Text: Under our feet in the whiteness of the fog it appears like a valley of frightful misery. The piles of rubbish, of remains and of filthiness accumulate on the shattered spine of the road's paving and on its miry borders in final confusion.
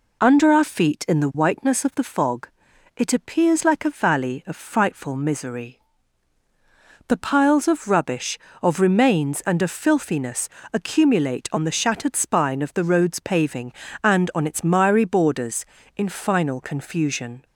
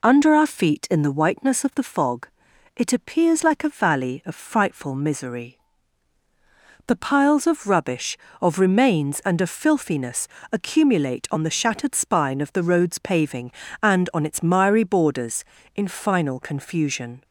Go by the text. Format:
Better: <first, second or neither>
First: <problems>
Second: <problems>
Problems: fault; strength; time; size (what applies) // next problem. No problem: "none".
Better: neither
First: pauses between "fog" and "it"; noticeable; at 2.4 s; 0.48 s long // pauses between "filthiness" and "accumulate"; slight; at 10.4 s; 0.24 s long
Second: pauses between "fog" and "it"; noticeable; at 2.2 s; 0.48 s long // pauses between "filthiness" and "accumulate"; slight; at 10.2 s; 0.24 s long